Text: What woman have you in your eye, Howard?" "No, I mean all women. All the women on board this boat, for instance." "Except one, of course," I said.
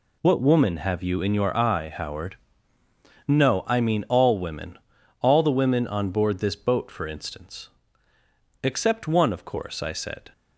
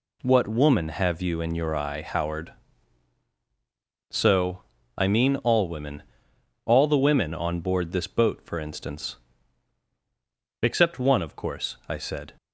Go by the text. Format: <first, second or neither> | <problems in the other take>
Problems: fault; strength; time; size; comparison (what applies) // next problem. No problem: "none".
first | says "So" for "No"; at 4.0 s